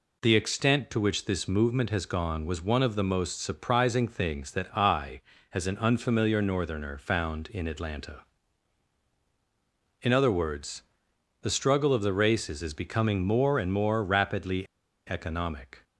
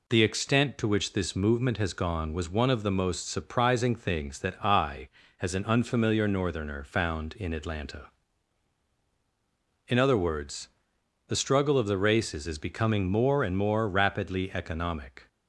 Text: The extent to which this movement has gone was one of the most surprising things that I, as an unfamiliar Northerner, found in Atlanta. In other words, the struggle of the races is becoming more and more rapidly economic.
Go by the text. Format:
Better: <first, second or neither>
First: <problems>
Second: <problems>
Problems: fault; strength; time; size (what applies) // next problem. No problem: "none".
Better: second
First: pauses between "rapidly" and "economic"; at 14.6 s; 0.43 s long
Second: none